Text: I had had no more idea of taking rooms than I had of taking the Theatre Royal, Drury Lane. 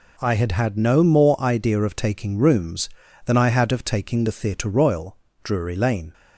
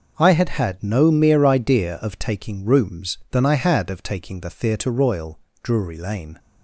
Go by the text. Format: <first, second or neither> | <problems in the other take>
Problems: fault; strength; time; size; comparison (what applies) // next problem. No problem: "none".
first | says "mere" for "more"; at 1.1 s